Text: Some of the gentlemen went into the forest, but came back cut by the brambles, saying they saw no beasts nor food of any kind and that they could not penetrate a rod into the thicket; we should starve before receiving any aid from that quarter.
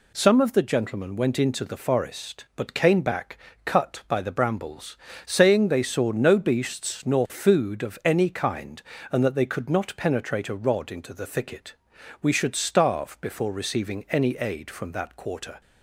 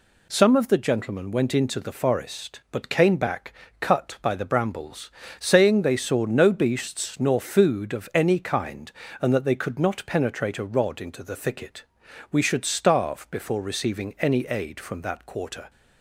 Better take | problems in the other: neither | pauses between "back" and "cut"; slight; the same in both

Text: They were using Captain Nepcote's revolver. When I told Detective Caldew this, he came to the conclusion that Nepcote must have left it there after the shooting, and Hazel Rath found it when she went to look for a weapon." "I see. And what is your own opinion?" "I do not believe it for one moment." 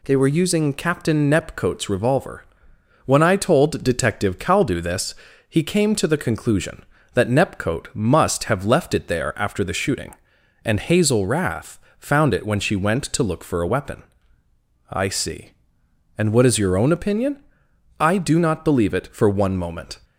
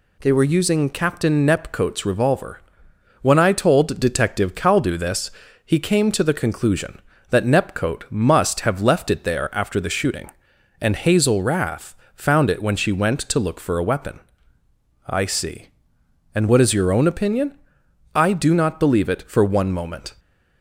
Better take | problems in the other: neither | pauses between "Rath" and "found"; slight; the same in both

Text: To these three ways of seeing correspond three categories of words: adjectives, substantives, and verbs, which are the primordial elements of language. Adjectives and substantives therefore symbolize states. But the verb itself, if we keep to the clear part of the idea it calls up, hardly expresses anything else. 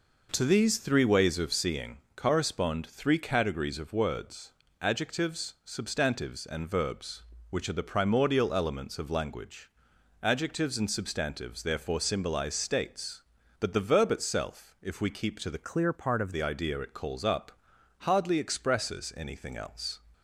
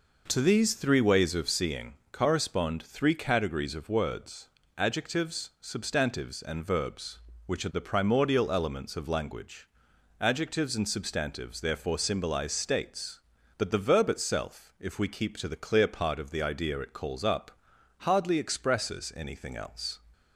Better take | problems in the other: second | pauses between "seeing" and "correspond"; slight; at 1.9 s; 0.16 s long; slight in the second // changes voice from "clear" to "of"; from 15.6 to 16.3 s; 0.7 s long

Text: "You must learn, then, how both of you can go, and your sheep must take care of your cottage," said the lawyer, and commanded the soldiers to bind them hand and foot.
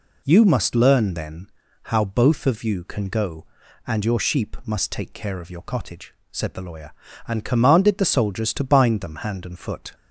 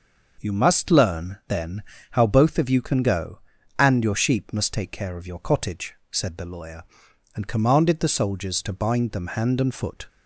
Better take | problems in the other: neither | none

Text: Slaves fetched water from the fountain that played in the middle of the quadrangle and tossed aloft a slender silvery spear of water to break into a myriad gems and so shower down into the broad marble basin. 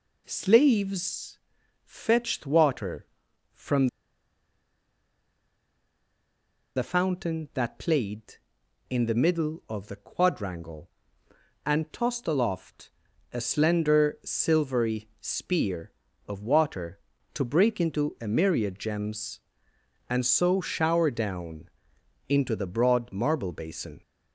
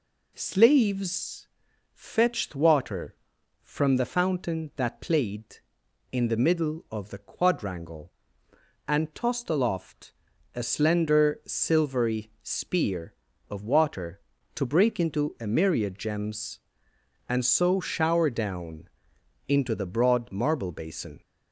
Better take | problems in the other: second | pauses between "Slaves" and "fetched"; noticeable; at 1.3 s; 0.48 s long; noticeable in the second // pauses between "from" and "the"; strong; at 3.8 s; 2.8 s long // pauses between "aloft" and "a"; at 12.8 s; 0.44 s long; also in the second // pauses between "down" and "into"; noticeable; at 21.6 s; 0.60 s long; noticeable in the second

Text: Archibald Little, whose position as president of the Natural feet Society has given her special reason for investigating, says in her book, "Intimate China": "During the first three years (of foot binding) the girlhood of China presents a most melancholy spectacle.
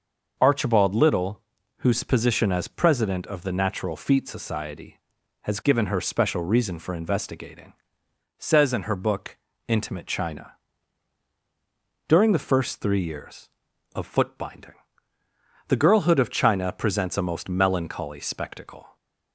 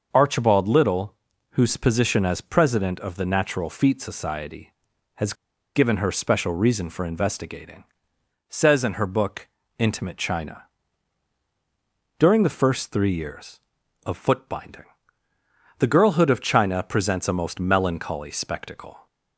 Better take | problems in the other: first | starts louder than the rest; noticeable; until 1.1 s; 6 dB; noticeable in the first // pauses between "has" and "given"; at 5.3 s; 0.42 s long

